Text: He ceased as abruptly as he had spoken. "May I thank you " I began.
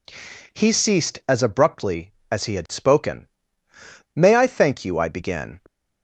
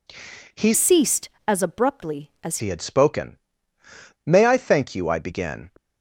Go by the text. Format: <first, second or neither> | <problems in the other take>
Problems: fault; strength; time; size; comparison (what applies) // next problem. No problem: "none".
first | changes voice from "ceased" to "as"; from 0.7 to 2.5 s; 1.8 s long